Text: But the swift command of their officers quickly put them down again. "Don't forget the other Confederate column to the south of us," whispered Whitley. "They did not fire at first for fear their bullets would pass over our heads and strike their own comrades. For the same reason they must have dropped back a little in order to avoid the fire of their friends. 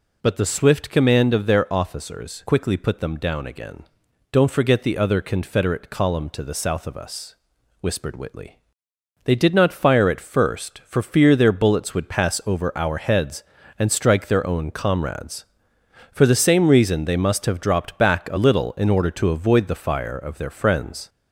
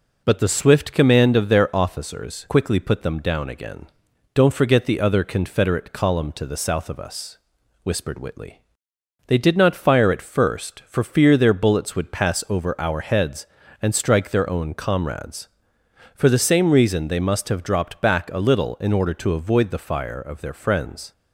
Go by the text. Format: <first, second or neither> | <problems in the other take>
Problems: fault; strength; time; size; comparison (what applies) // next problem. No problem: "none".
second | gets louder; slight; throughout; 3 dB